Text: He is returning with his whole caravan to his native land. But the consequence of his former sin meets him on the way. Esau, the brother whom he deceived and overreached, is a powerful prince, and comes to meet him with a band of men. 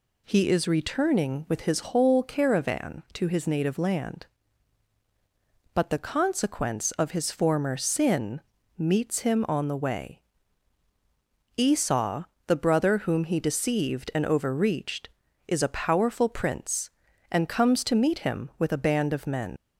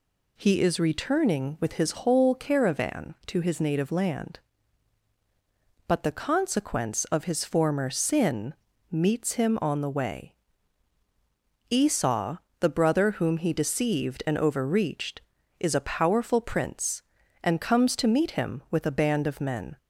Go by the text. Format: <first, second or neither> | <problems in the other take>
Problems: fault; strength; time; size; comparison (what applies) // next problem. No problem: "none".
second | pauses between "sin" and "meets"; at 8.3 s; 0.38 s long; also in the second // leaves "men" unfinished; at 19.5 s; 75 ms